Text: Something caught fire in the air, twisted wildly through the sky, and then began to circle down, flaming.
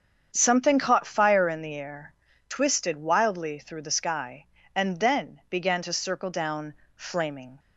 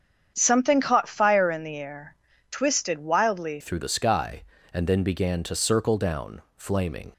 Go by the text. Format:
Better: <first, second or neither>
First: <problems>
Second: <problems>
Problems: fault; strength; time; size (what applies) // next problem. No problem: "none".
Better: first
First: starts louder than the rest; strong; until 1.3 s; 7.5 dB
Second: starts louder than the rest; strong; until 1.3 s; 8 dB // changes voice at "through"; from 3.6 s on; 3.5 s long